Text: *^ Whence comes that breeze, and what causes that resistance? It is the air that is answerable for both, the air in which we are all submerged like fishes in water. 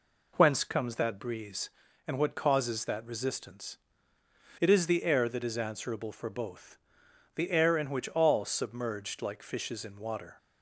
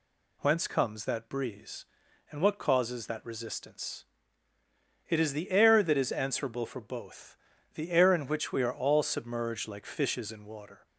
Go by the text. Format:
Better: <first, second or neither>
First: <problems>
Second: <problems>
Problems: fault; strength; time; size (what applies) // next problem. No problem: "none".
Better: second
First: skips "we are"; at 8.0 s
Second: none